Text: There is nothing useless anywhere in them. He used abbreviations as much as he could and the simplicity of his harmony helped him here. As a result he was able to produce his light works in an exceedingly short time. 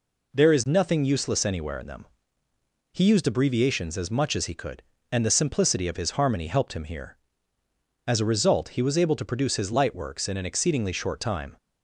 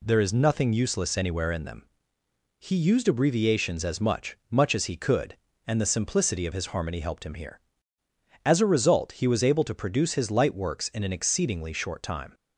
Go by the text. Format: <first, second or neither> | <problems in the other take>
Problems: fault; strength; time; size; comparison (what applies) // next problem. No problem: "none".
first | says "much" twice; at 4.5 s